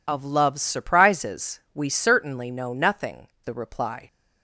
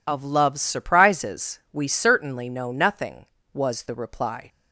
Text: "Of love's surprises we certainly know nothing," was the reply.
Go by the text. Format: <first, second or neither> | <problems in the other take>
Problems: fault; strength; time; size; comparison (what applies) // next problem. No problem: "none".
second | pauses between "surprises" and "we"; slight; at 1.5 s; 0.16 s long // skips "was"; at 3.3 s